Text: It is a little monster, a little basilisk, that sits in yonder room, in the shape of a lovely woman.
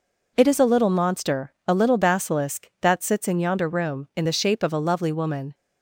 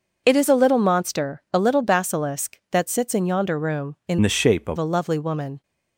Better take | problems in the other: first | changes voice from "the" to "of"; from 4.2 to 4.7 s; 0.5 s long

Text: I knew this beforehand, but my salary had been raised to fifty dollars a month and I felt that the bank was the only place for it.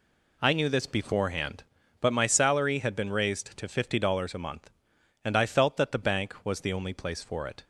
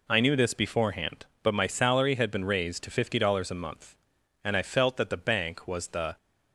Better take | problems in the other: first | stops before "only place for it"; at 6.1 s

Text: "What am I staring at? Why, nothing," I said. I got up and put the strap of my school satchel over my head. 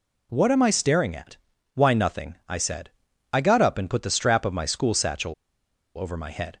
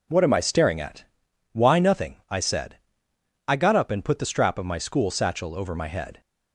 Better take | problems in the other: second | pauses between "satchel" and "over"; noticeable; at 5.3 s; 0.63 s long

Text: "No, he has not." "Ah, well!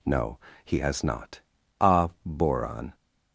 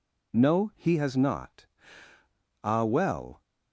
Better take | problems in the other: second | says "boron" for "well"; at 2.2 s

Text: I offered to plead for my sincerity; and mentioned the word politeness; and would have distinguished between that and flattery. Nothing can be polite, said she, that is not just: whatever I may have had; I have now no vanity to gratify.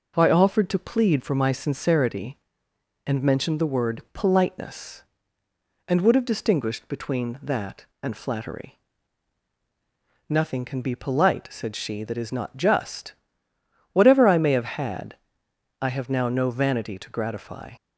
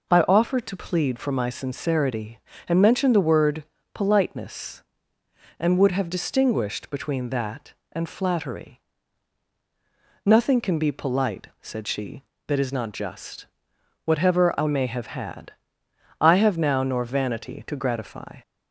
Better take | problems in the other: first | pauses between "word" and "politeness"; slight; at 3.6 s; 0.28 s long // says "nor" for "no"; at 16.8 s

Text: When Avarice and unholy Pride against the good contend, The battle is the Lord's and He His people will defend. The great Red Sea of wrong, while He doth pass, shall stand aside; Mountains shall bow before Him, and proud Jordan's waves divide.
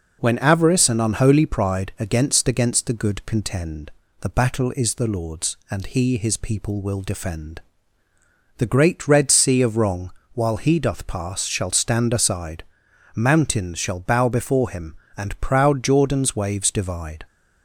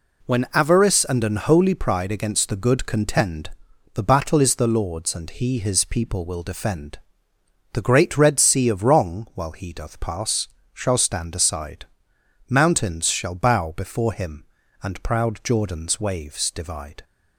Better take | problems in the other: second | says "against" twice; at 2.4 s

